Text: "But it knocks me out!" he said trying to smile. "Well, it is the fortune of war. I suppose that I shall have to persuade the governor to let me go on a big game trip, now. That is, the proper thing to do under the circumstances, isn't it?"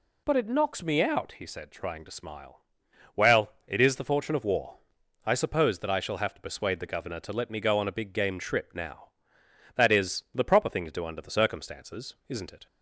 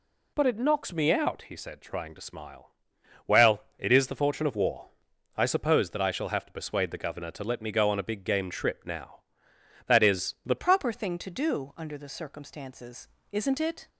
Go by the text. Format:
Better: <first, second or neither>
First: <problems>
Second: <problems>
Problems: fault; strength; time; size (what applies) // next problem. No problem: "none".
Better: first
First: none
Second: changes voice at "proper"; from 10.5 s on; 3.3 s long